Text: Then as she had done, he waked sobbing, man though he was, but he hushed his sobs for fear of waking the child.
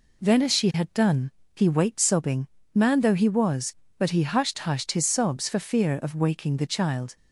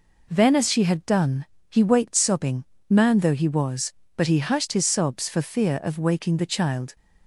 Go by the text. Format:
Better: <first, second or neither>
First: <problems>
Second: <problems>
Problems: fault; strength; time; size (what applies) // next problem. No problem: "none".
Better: second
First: says "hushed" twice; at 4.5 s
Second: none